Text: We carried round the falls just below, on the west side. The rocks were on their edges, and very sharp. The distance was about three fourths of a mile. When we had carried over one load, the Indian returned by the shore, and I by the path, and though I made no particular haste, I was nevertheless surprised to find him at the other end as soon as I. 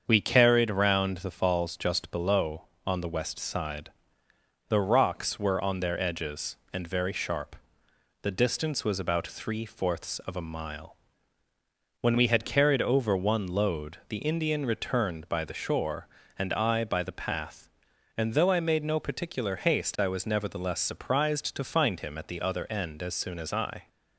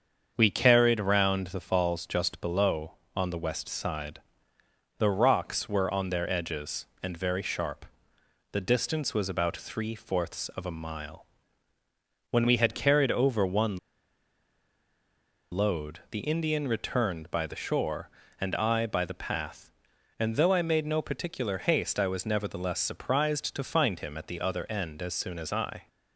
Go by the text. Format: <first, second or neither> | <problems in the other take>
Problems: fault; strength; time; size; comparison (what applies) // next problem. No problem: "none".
first | starts louder than the rest; strong; until 1.3 s; 7 dB; strong in the first // pauses between "one" and "load"; strong; at 13.7 s; 1.7 s long